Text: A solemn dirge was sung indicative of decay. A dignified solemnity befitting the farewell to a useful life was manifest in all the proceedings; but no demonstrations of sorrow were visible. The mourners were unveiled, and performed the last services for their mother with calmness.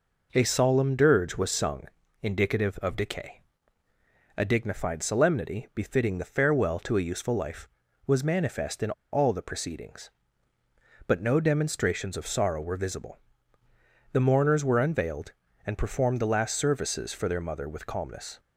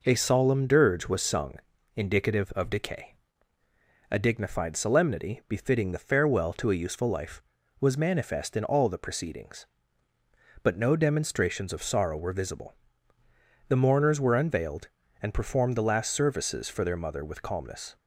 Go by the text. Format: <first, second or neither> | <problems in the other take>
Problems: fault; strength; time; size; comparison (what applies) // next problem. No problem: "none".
second | pauses between "sung" and "indicative"; slight; at 1.8 s; 0.36 s long; also in the second // pauses between "in" and "all"; slight; at 8.9 s; 0.20 s long